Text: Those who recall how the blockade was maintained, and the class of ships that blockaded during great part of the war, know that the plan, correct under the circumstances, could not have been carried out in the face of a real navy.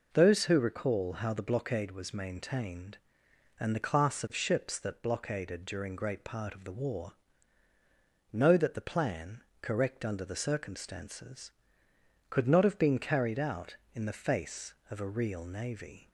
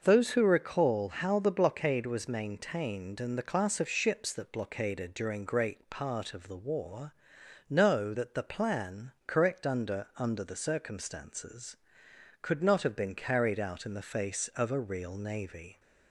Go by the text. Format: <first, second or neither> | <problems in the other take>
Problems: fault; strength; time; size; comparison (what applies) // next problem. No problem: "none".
first | starts louder than the rest; until 1.0 s; 6.5 dB // says "under" twice; at 10.1 s